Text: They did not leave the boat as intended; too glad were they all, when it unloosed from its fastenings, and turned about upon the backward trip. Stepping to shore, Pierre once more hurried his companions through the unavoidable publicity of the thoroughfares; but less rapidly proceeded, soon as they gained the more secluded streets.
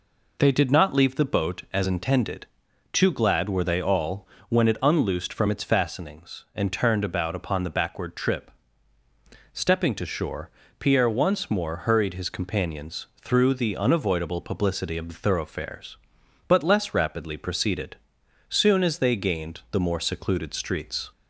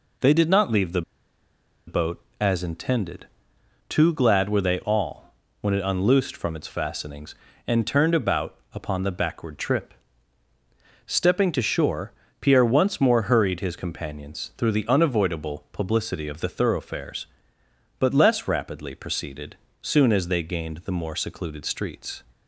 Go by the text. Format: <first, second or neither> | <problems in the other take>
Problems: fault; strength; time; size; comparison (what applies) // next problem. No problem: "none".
first | pauses between "the" and "boat"; noticeable; at 1.0 s; 0.85 s long // pauses between "about" and "upon"; slight; at 8.5 s; 0.16 s long